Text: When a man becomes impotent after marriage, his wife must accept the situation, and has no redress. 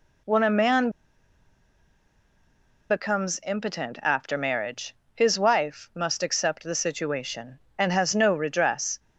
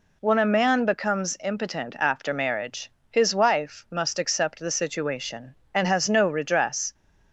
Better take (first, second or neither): second